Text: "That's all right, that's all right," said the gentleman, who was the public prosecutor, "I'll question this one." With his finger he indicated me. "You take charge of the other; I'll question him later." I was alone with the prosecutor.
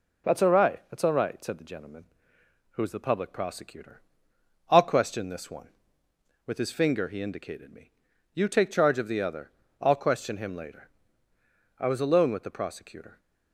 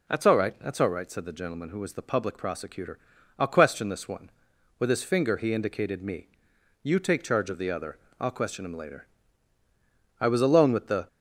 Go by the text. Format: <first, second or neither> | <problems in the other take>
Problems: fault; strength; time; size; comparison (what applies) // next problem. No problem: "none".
first | stops before "prosecutor"; at 11.0 s